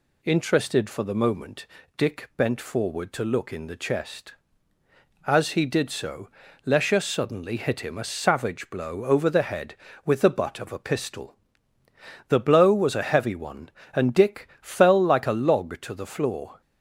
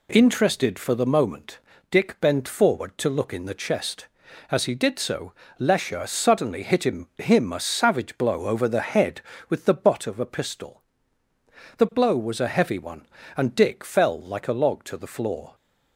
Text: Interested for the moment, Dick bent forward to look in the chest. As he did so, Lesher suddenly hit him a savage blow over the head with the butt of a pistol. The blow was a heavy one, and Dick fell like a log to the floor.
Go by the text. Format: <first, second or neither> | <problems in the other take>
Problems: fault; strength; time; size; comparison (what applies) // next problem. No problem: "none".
first | says "him" twice; at 7.1 s